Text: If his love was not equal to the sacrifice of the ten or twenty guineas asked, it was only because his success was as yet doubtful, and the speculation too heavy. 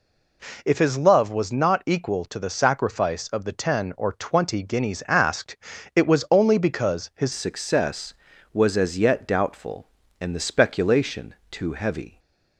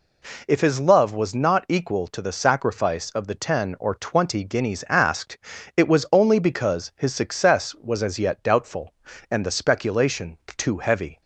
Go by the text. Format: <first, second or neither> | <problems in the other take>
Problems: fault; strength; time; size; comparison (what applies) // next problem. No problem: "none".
second | changes voice at "success"; from 7.3 s on; 4.8 s long // pauses between "speculation" and "too"; slight; at 11.3 s; 0.16 s long; slight in the second // stays silent after the last word; slight; from 12.0 s on; 0.5 s long